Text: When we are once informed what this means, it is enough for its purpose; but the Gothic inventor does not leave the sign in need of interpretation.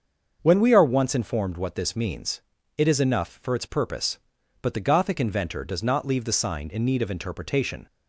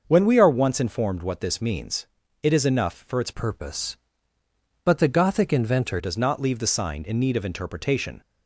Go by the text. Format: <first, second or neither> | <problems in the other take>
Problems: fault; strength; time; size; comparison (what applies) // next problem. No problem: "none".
first | starts louder than the rest; until 1.0 s; 6 dB; also in the first // changes voice from "purpose" to "inventor"; from 3.3 to 5.9 s; 2.6 s long